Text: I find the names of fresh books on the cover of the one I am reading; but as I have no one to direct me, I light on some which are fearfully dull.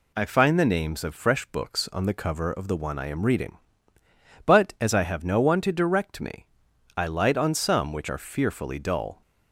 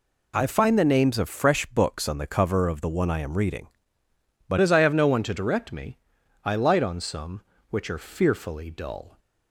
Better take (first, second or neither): first